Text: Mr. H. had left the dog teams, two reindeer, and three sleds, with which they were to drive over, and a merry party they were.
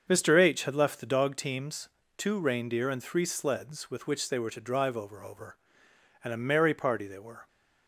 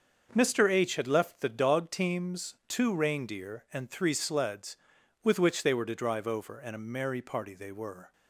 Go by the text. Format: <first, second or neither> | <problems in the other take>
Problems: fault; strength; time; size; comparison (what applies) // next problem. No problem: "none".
second | starts louder than the rest; until 1.0 s; 7 dB; also in the second // says "over" twice; at 5.2 s